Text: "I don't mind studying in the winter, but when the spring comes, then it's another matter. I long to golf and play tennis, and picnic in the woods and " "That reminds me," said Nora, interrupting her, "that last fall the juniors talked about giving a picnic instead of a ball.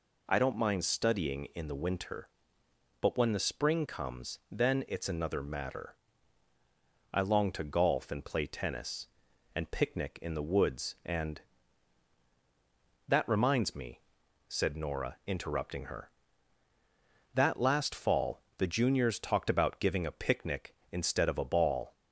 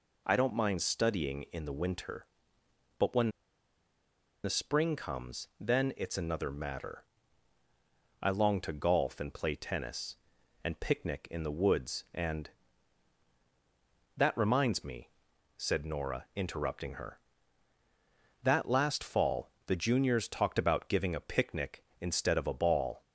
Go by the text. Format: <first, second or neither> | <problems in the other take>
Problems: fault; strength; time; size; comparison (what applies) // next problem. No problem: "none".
first | pauses between "when" and "the"; at 3.2 s; 1.1 s long // pauses between "fall" and "the"; slight; at 19.5 s; 0.16 s long; slight in the first